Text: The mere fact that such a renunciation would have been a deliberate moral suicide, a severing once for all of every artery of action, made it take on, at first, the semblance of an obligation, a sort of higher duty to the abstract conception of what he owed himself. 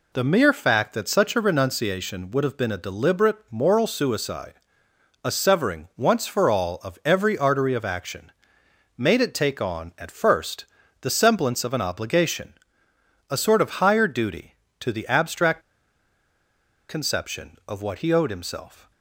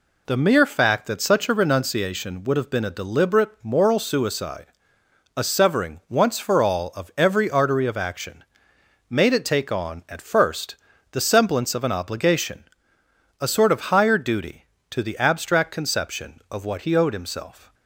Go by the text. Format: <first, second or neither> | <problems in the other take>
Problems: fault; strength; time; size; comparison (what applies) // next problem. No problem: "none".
second | pauses between "abstract" and "conception"; strong; at 15.6 s; 1.2 s long